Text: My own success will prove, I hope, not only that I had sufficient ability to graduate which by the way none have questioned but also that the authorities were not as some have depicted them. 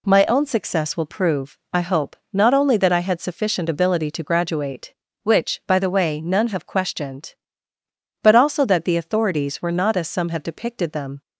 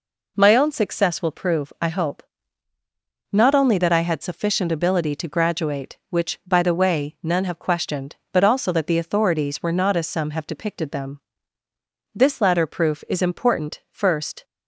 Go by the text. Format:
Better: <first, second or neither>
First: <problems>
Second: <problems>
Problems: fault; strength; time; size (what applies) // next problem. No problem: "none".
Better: first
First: none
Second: goes on to say "This latter proof is important first"; strong; from 12.1 s on; 2.3 s long